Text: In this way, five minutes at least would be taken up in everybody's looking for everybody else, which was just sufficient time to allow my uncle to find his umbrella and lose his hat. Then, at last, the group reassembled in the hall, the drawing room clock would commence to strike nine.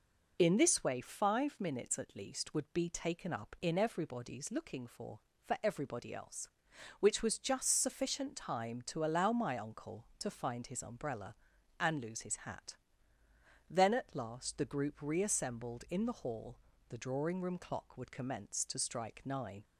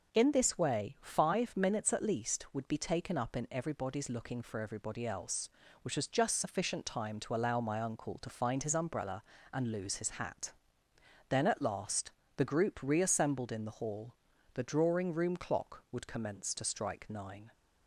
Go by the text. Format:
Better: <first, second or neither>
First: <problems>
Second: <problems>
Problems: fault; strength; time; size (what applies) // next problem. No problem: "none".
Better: second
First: says "for" twice; at 5.4 s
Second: none